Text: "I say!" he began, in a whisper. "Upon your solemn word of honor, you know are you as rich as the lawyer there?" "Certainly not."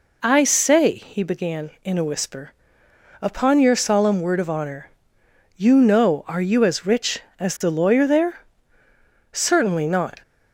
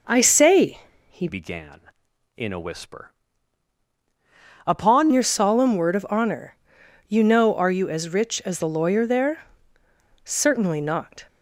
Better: first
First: none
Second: changes voice from "began" to "Upon"; from 1.2 to 5.0 s; 3.8 s long

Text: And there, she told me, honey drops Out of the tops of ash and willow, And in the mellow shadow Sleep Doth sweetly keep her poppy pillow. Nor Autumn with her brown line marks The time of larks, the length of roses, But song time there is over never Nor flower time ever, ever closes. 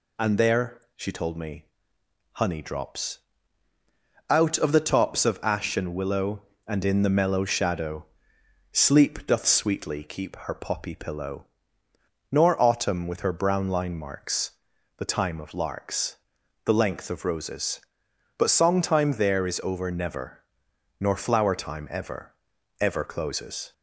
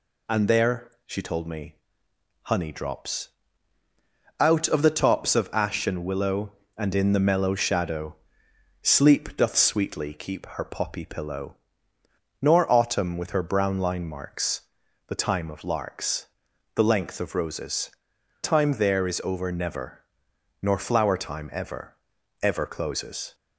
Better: first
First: pauses between "drops" and "Out"; at 3.1 s; 1.1 s long // pauses between "shadow" and "Sleep"; noticeable; at 8.0 s; 0.66 s long // pauses between "marks" and "The"; noticeable; at 14.5 s; 0.46 s long // pauses between "never" and "Nor"; noticeable; at 20.4 s; 0.56 s long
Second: pauses between "drops" and "Out"; at 3.2 s; 1.1 s long // pauses between "shadow" and "Sleep"; noticeable; at 8.1 s; 0.66 s long // pauses between "marks" and "The"; noticeable; at 14.6 s; 0.46 s long // skips "But song"; at 18.1 s // pauses between "never" and "Nor"; noticeable; at 20.0 s; 0.58 s long

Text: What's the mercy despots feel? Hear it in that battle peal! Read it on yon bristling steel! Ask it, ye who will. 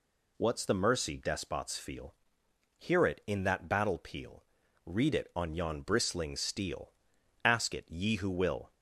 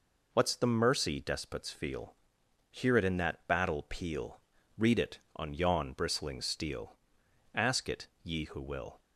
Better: neither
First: none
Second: none

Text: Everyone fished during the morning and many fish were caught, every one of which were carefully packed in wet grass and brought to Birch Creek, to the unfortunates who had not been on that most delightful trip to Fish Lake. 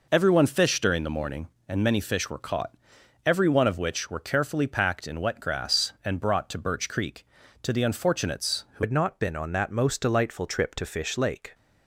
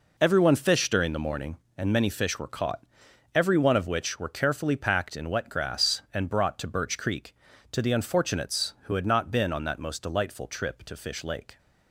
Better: second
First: changes voice at "had"; from 8.8 s on; 2.7 s long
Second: none

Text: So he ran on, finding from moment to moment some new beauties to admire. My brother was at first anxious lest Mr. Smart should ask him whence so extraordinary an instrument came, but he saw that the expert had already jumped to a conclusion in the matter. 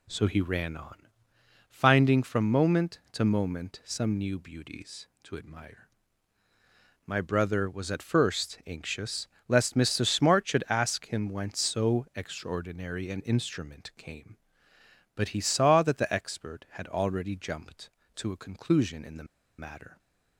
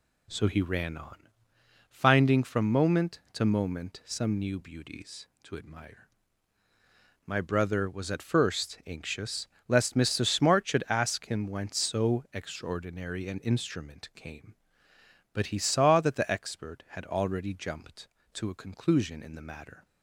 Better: second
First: pauses between "anxious" and "lest"; slight; at 9.2 s; 0.18 s long // pauses between "the" and "matter"; slight; at 19.2 s; 0.33 s long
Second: pauses between "anxious" and "lest"; slight; at 9.4 s; 0.18 s long

